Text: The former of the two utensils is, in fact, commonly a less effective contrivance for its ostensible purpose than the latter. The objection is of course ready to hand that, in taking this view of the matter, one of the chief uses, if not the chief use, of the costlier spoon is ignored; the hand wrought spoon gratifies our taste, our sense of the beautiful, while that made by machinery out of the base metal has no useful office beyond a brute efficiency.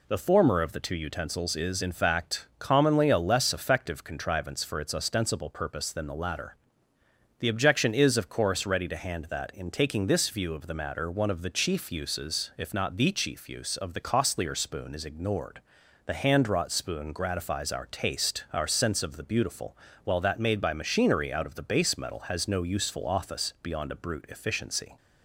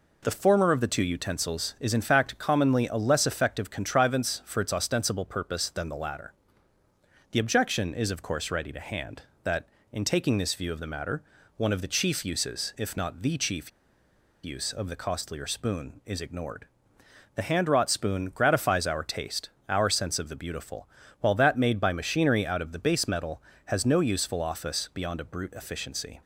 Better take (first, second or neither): first